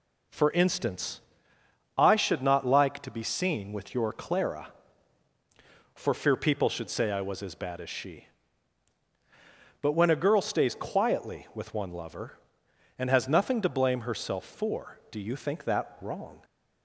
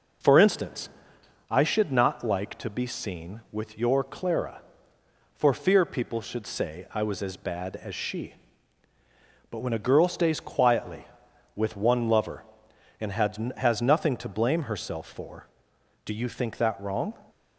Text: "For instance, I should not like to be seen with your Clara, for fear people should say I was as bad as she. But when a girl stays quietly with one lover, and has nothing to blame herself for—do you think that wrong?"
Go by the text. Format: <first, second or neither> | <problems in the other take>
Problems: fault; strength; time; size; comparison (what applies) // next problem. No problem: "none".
first | says "has" twice; at 13.5 s